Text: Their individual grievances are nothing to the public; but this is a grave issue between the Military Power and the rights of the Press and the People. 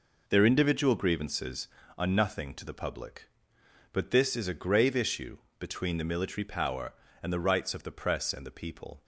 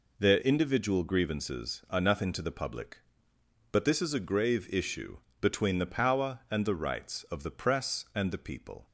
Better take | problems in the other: first | pauses between "issue" and "between"; slight; at 5.1 s; 0.24 s long; slight in the first // skips "Military"; at 5.9 s

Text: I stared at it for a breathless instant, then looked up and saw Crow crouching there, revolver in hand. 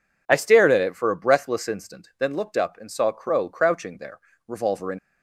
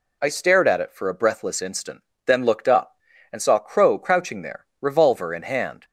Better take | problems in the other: second | stops before "hand"; at 4.9 s

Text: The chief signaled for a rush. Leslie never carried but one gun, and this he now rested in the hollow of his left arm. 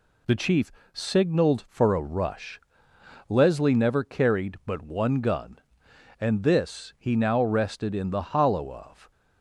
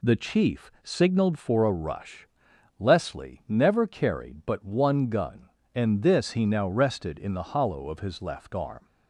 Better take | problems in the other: second | pauses between "chief" and "signaled"; slight; at 0.7 s; 0.22 s long // stops before "his left arm"; at 9.1 s

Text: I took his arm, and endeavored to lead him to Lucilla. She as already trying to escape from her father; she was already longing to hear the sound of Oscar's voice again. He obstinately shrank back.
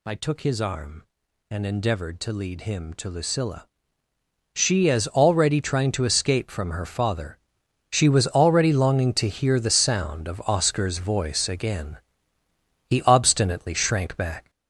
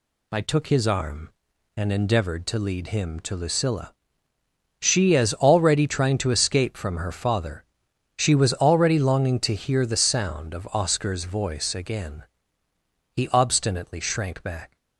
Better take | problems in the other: second | gets louder; noticeable; throughout; 5 dB

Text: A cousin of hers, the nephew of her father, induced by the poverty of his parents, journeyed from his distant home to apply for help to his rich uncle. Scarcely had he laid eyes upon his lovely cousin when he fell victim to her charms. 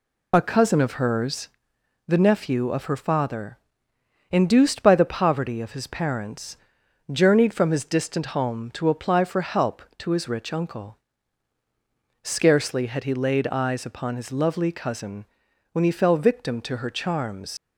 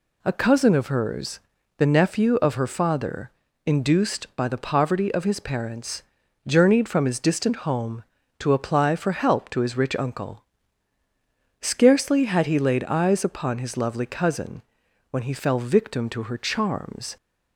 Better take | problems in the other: second | pauses between "cousin" and "when"; noticeable; at 15.2 s; 0.46 s long; noticeable in the second // leaves "charms" unfinished; at 17.5 s; 55 ms

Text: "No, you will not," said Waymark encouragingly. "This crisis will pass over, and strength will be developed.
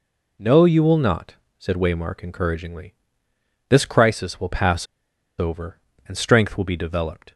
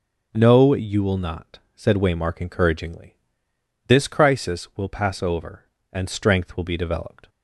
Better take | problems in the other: second | pauses between "pass" and "over"; noticeable; at 4.8 s; 0.53 s long

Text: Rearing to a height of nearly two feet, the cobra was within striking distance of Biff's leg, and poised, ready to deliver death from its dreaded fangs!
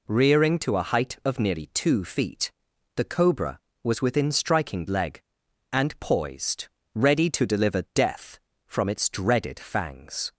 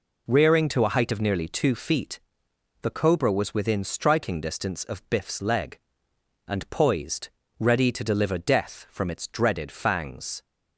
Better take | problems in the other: second | skips "distance of Biff's"; at 4.8 s

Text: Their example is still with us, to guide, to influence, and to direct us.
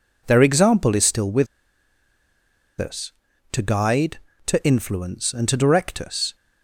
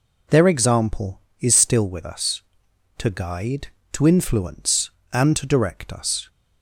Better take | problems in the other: second | pauses between "with" and "us"; strong; at 1.4 s; 1.3 s long

